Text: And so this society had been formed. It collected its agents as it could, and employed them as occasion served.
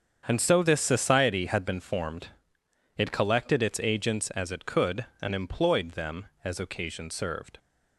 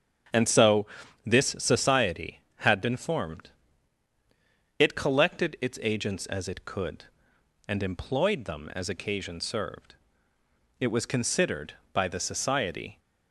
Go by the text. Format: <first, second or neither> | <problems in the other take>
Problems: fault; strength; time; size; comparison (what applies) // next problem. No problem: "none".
first | starts louder than the rest; strong; until 1.7 s; 7.5 dB; strong in the first // pauses between "so" and "this"; at 0.8 s; 0.40 s long // goes on to say "It was considered by the society"; strong; from 10.7 s on; 2.2 s long